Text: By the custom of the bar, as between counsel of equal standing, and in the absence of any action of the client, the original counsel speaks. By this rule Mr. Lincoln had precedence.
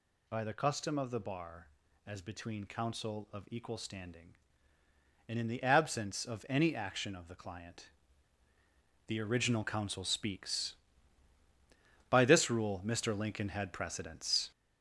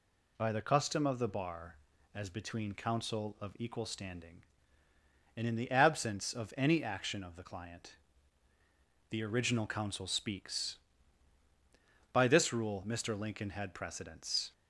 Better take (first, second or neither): second